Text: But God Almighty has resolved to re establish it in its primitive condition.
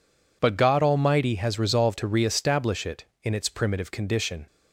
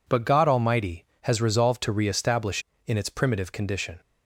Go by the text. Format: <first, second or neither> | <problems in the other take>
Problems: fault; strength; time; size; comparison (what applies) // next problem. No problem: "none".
first | skips "it"; at 2.7 s